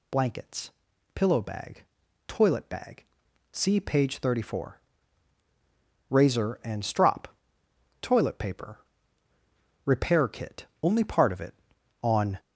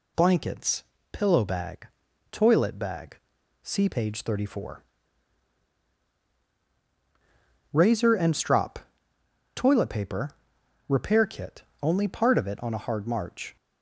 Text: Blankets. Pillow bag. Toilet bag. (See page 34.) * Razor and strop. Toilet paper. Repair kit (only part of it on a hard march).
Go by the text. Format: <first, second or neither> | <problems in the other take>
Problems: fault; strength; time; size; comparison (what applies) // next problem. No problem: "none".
second | stops before "a hard march"; at 12.3 s